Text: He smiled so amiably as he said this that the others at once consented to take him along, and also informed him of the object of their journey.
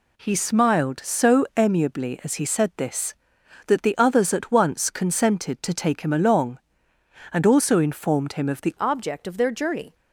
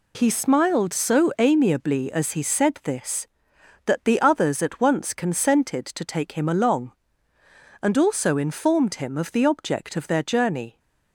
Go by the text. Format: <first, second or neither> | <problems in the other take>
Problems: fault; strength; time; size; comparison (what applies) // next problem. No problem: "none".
second | changes voice at "object"; from 8.7 s on; 1.2 s long